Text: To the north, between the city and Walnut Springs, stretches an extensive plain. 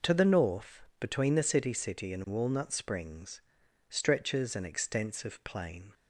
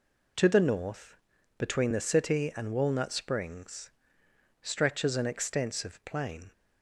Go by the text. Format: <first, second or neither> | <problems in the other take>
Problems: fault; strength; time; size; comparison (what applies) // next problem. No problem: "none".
second | says "city" twice; at 1.7 s